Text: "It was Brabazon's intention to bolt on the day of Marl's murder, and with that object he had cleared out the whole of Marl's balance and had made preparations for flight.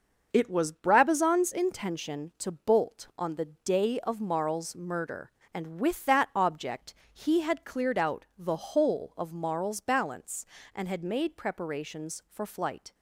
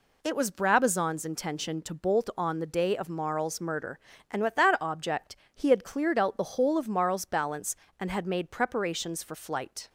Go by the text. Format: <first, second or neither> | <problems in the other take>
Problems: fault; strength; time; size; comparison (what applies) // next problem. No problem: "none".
neither | pauses between "object" and "he"; slight; the same in both